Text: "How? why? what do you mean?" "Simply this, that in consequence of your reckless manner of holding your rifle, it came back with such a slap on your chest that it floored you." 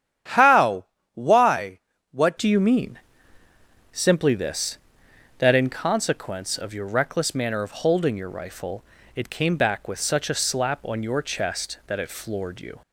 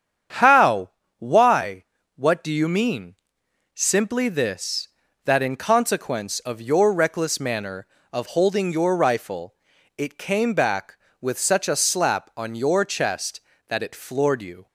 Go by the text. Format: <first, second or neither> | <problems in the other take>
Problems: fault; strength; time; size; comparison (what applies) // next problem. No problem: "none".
second | starts louder than the rest; strong; until 1.5 s; 9.5 dB; strong in the second // changes voice at "do"; from 2.3 s on; 10.5 s long